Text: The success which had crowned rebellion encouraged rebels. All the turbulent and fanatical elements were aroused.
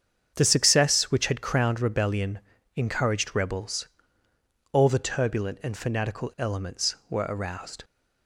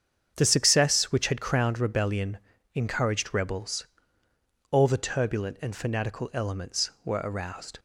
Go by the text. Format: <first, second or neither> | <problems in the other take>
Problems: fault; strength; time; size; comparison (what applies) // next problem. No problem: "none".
neither | starts louder than the rest; strong; the same in both // pauses between "rebellion" and "encouraged"; slight; the same in both